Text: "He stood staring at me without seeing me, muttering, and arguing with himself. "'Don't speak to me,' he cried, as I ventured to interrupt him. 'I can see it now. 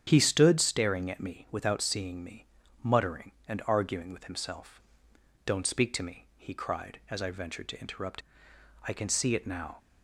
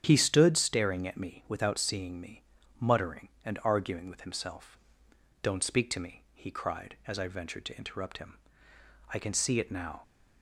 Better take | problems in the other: second | starts louder than the rest; strong; until 1.0 s; 8.5 dB; strong in the second // skips "him"; at 8.5 s

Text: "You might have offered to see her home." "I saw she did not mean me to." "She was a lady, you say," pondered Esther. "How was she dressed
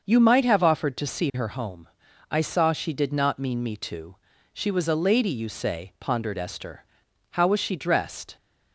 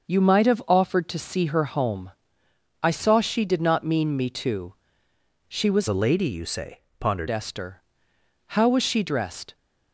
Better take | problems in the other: first | starts louder than the rest; noticeable; until 1.1 s; 6 dB; also in the first // changes voice from "a" to "pondered"; from 5.8 to 7.2 s; 1.4 s long

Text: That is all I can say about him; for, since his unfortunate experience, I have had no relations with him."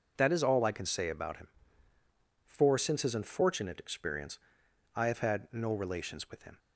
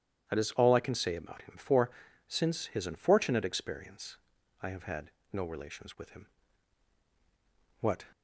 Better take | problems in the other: first | starts louder than the rest; strong; until 1.3 s; 10 dB // pauses between "had" and "no"; slight; at 5.1 s; 0.20 s long // goes on to say "What"; slight; from 7.8 s on; 0.24 s long

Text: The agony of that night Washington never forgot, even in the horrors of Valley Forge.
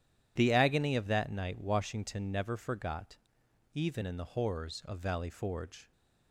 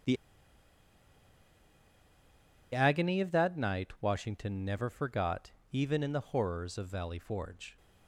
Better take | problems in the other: first | pauses between "The" and "agony"; strong; at 0.1 s; 2.5 s long

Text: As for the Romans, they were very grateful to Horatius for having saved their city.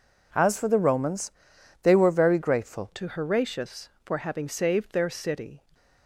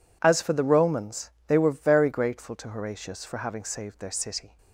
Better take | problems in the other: second | changes voice at "to"; from 2.9 s on; 2.7 s long

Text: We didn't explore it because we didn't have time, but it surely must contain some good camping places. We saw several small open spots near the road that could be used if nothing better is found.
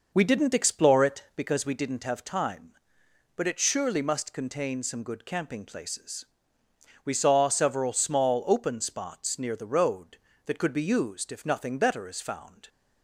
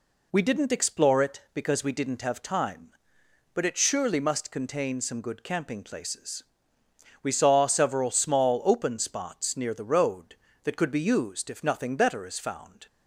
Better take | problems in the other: second | starts louder than the rest; noticeable; until 1.5 s; 5.5 dB

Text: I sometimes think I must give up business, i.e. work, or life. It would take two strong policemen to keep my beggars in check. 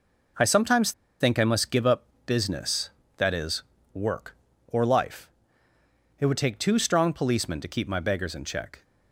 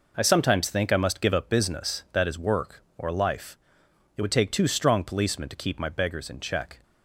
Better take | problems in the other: second | pauses between "sometimes" and "think"; slight; at 0.9 s; 0.29 s long // pauses between "up" and "business"; slight; at 2.0 s; 0.22 s long

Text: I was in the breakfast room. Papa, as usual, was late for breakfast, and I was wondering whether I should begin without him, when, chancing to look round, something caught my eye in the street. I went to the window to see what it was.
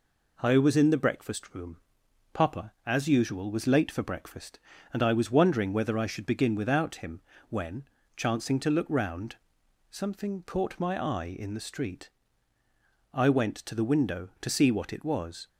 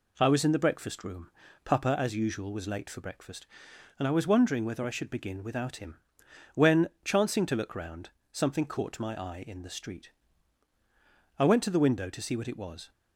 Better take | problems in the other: neither | none

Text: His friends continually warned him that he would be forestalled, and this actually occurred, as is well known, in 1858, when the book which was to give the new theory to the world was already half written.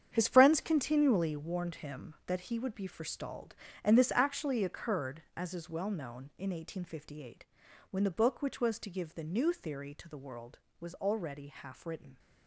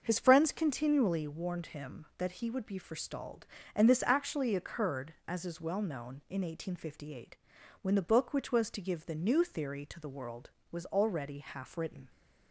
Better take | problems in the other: second | gets quieter; strong; throughout; 11.5 dB // starts louder than the rest; strong; until 1.1 s; 8.5 dB; also in the second

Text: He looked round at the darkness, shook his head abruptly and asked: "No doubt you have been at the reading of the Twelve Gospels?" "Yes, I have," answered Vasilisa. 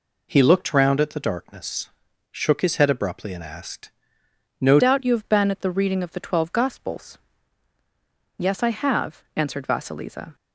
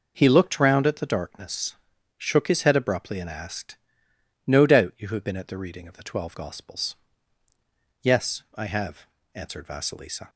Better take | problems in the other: second | changes voice at "doubt"; from 4.7 s on; 5.6 s long

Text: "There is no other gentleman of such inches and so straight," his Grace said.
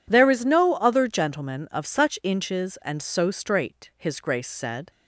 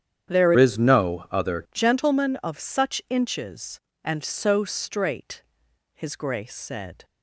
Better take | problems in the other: first | starts louder than the rest; strong; until 1.3 s; 9 dB // changes voice from "is" to "other"; from 0.5 to 1.6 s; 1.1 s long

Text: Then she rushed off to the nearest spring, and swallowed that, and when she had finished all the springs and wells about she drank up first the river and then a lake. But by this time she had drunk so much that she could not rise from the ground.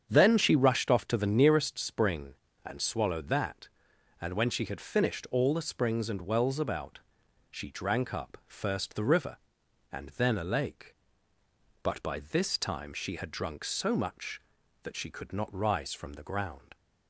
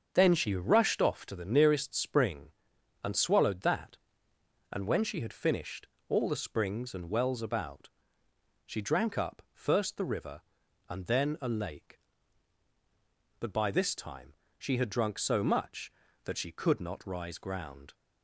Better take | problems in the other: first | starts louder than the rest; until 1.1 s; 7 dB; strong in the first // pauses between "finished" and "all"; slight; at 5.8 s; 0.22 s long // pauses between "about" and "she"; noticeable; at 7.8 s; 0.74 s long; noticeable in the first // pauses between "time" and "she"; slight; at 14.3 s; 0.24 s long // skips "from the"; at 17.3 s

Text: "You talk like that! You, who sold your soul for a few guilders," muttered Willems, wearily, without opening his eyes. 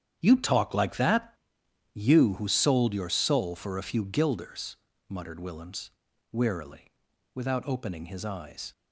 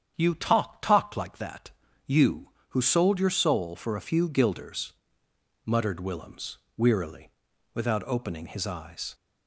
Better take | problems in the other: first | starts louder than the rest; strong; until 1.1 s; 8.5 dB; strong in the first // says "talk" twice; at 0.8 s

